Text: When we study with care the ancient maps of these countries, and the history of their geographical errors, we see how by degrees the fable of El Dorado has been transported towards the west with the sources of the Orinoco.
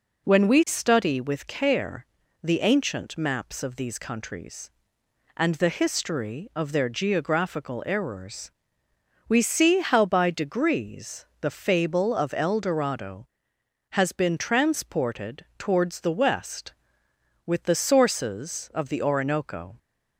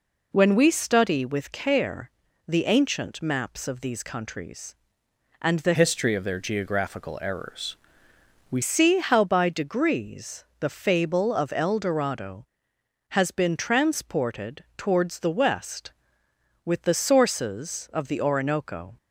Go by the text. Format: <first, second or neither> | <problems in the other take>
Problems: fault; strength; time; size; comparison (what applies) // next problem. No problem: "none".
first | pauses between "care" and "the"; at 2.1 s; 0.38 s long; also in the first // changes voice from "history" to "we"; from 5.7 to 8.6 s; 2.9 s long // pauses between "degrees" and "the"; slight; at 10.4 s; 0.16 s long; slight in the first